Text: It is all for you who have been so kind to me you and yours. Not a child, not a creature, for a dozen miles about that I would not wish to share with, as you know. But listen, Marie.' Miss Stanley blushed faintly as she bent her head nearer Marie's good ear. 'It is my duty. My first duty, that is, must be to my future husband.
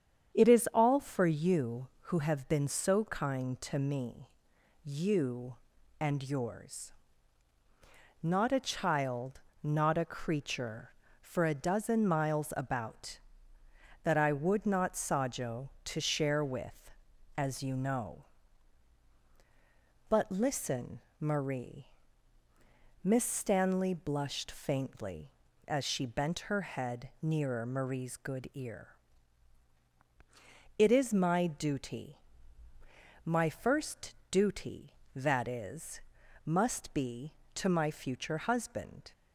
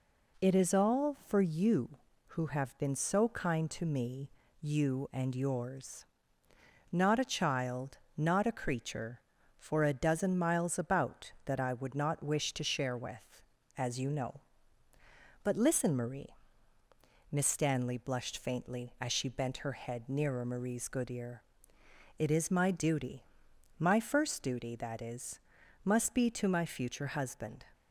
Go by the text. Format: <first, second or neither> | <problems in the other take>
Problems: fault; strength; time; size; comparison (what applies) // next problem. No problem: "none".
second | starts louder than the rest; strong; until 1.4 s; 8.5 dB // pauses between "me" and "you"; noticeable; at 4.2 s; 0.54 s long; slight in the second // says "sajo" for "wish"; at 14.9 s // pauses between "first" and "duty"; slight; at 34.1 s; 0.16 s long